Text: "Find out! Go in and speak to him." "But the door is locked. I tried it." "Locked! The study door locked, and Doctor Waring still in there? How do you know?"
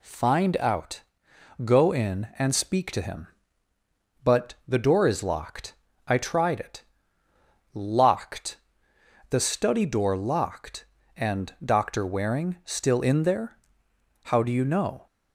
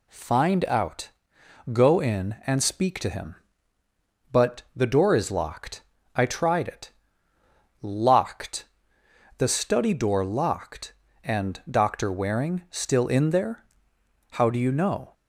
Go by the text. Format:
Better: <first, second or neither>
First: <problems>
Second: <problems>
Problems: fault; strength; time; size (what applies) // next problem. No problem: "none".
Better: neither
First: none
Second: none